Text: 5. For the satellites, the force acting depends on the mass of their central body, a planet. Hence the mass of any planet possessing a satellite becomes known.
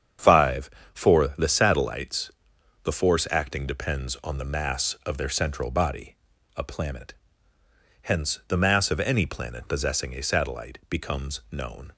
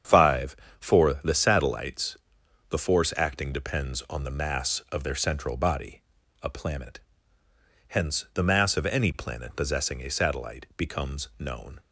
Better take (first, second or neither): neither